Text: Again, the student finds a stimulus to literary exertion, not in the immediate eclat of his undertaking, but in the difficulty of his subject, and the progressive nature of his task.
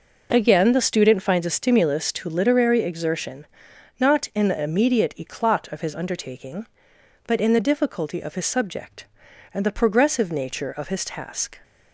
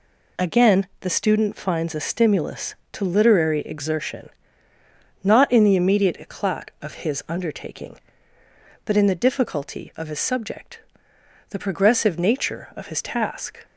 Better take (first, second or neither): first